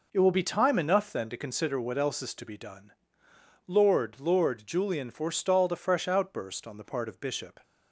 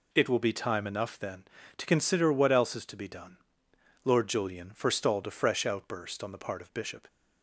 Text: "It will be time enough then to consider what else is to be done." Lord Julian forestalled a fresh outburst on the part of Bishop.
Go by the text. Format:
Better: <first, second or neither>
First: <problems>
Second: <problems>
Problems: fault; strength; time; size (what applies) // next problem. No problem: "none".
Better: second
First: says "Lord" twice; at 4.1 s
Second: none